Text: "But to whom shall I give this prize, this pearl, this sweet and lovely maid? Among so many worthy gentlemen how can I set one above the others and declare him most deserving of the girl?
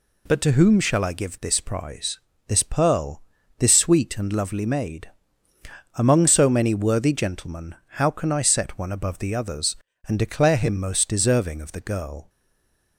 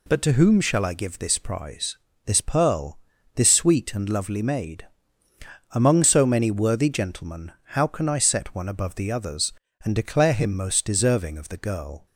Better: second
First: pauses between "gentlemen" and "how"; slight; at 7.7 s; 0.18 s long // stays silent after the last word; slight; from 12.2 s on; 0.7 s long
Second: pauses between "gentlemen" and "how"; slight; at 7.5 s; 0.18 s long

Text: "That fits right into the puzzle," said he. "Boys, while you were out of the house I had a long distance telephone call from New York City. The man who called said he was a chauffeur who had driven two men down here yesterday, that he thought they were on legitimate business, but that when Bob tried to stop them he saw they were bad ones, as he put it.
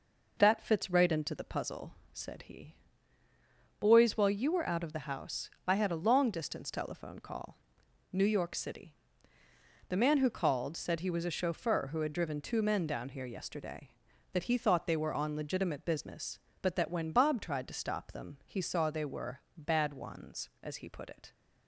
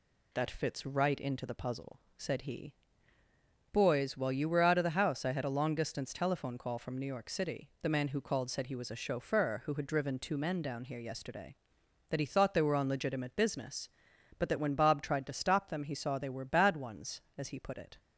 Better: second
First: pauses between "house" and "I"; slight; at 5.4 s; 0.16 s long // skips "from"; at 7.8 s // pauses between "were" and "bad"; slight; at 19.3 s; 0.16 s long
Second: none

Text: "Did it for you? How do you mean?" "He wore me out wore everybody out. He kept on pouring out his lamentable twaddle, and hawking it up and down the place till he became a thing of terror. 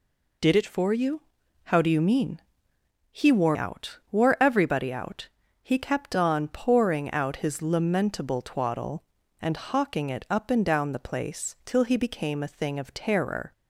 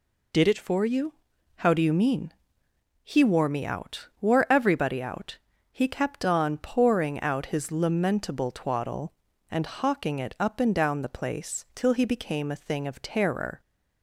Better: second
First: skips "me"; at 3.5 s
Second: none

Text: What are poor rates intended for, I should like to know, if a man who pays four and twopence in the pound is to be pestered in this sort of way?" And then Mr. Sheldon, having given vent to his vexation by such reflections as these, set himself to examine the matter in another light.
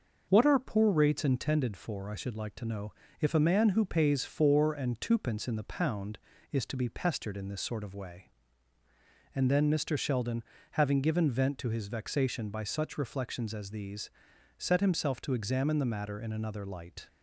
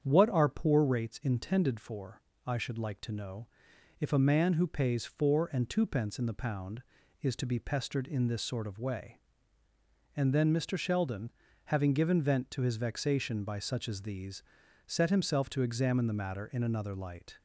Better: first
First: starts louder than the rest; noticeable; until 1.3 s; 6 dB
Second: starts louder than the rest; strong; until 1.0 s; 8 dB // skips "reflections"; at 13.8 s

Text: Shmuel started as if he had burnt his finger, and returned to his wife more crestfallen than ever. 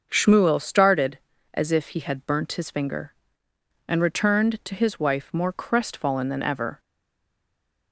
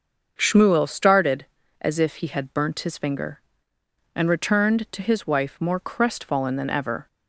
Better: second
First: starts louder than the rest; until 1.1 s; 6 dB // stays silent after the last word; from 6.7 s on; 1.2 s long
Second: starts louder than the rest; until 1.3 s; 6 dB

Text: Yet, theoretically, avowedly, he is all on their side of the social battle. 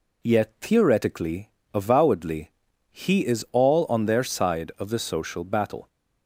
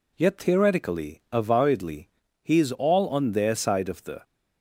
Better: first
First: none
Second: stops before "social battle"; at 4.2 s

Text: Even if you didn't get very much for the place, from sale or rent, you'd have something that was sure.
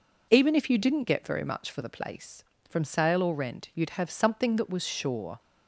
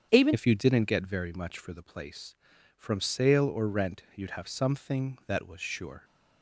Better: first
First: none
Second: starts louder than the rest; strong; until 1.1 s; 8 dB // changes voice at "if"; from 0.3 s on; 5.7 s long

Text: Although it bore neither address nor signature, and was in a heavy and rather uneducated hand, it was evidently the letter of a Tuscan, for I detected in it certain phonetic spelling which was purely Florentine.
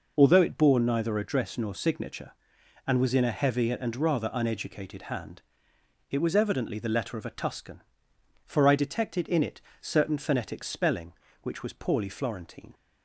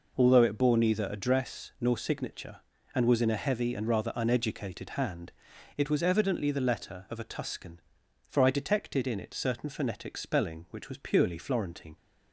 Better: second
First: pauses between "it" and "certain"; slight; at 9.6 s; 0.18 s long // says "poorly" for "purely"; at 11.7 s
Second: none

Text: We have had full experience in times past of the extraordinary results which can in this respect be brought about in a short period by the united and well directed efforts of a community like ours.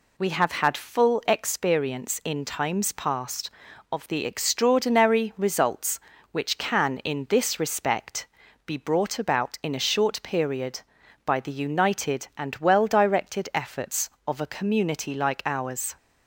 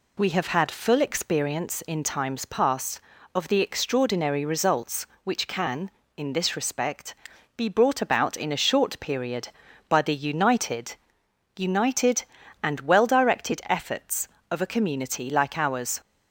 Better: first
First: pauses between "respect" and "be"; at 8.2 s; 0.38 s long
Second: pauses between "respect" and "be"; at 7.1 s; 0.42 s long // says "united" twice; at 11.5 s

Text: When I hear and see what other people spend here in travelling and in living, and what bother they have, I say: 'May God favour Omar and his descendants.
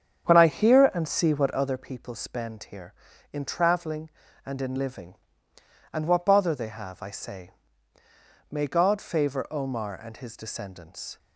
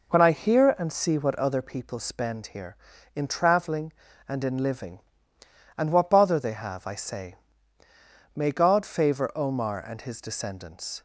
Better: second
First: starts louder than the rest; strong; until 1.8 s; 8 dB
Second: none

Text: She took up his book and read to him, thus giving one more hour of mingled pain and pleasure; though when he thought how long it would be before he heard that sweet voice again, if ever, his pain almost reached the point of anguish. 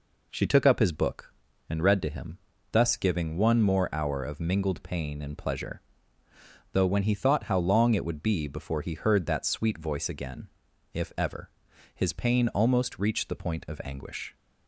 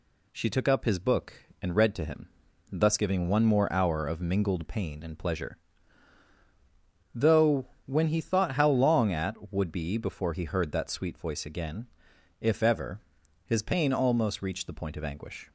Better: first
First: none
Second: pauses between "though" and "when"; slight; at 7.6 s; 0.20 s long // says "at" for "it"; at 9.1 s

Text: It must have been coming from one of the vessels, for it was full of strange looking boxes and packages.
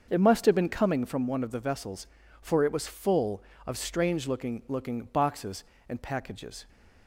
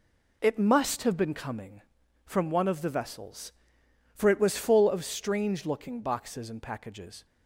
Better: second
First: starts louder than the rest; until 1.1 s; 6.5 dB // says "looking" twice; at 4.6 s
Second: none

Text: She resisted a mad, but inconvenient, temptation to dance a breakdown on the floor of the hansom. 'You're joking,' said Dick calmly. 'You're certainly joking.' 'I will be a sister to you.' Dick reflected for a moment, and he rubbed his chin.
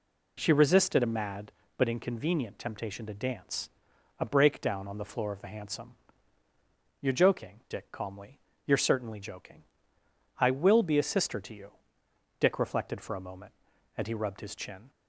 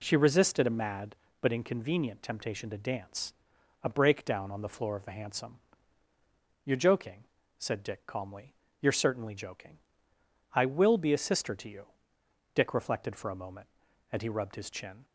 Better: second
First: pauses between "dance" and "a"; noticeable; at 3.7 s; 0.50 s long // skips "said"; at 7.6 s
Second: pauses between "dance" and "a"; noticeable; at 3.3 s; 0.50 s long

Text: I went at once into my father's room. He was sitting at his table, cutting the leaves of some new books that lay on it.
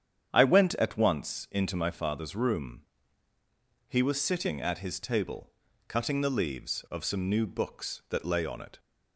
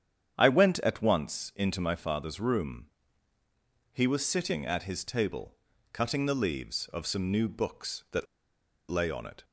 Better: first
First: starts louder than the rest; strong; until 1.3 s; 8.5 dB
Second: starts louder than the rest; strong; until 1.3 s; 8.5 dB // pauses between "that" and "lay"; noticeable; at 8.2 s; 0.64 s long

